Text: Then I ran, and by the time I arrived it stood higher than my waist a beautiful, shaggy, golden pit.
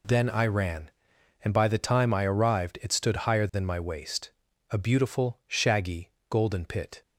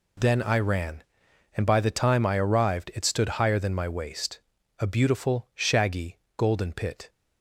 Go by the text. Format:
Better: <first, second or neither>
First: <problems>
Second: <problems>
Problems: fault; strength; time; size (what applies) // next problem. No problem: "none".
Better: neither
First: pauses between "waist" and "a"; at 4.3 s; 0.40 s long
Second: pauses between "waist" and "a"; at 4.4 s; 0.40 s long